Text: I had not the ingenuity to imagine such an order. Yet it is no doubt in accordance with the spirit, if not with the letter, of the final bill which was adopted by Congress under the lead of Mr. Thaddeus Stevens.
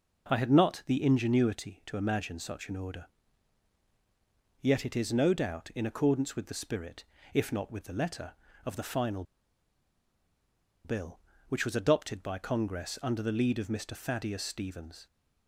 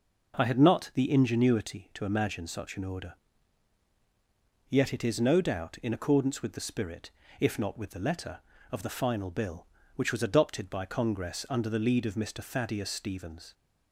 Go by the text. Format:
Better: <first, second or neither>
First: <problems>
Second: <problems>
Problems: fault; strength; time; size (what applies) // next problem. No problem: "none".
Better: second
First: pauses between "final" and "bill"; strong; at 9.2 s; 1.6 s long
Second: none